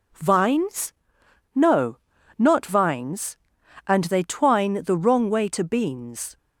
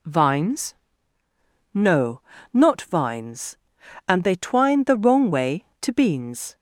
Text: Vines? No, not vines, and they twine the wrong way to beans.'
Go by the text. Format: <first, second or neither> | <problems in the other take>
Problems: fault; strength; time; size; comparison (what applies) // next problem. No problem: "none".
neither | none